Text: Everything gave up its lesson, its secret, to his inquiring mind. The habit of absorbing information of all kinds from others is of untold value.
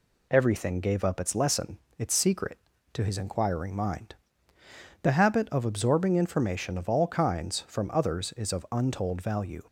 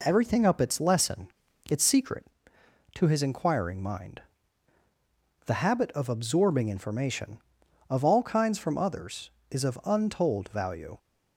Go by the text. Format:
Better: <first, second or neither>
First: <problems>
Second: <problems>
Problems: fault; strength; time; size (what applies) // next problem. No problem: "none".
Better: first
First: none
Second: skips "gave"; at 0.4 s